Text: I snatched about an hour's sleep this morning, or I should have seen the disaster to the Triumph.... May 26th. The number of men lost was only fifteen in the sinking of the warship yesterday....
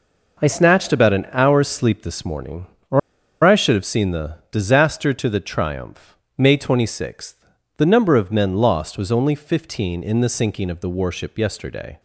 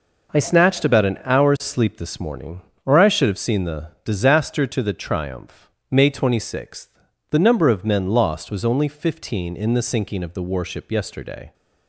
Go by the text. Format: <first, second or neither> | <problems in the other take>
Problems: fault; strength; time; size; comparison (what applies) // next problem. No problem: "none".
second | pauses between "or" and "I"; at 2.9 s; 0.44 s long